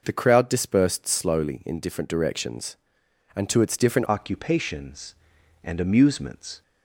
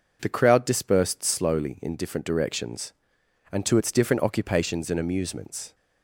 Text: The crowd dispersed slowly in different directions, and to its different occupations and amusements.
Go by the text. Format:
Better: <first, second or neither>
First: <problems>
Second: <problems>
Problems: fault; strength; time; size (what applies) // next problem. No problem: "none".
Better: second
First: changes voice at "occupations"; from 4.0 s on; 2.6 s long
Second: none